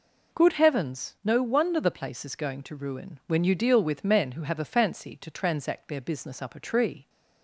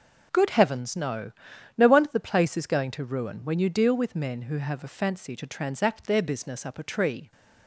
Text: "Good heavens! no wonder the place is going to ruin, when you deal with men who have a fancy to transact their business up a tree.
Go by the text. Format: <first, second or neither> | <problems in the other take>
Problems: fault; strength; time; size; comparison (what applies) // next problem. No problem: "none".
first | says "no" twice; at 1.7 s